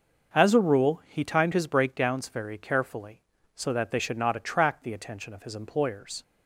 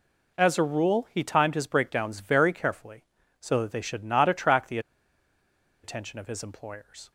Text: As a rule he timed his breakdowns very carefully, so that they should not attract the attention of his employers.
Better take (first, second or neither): first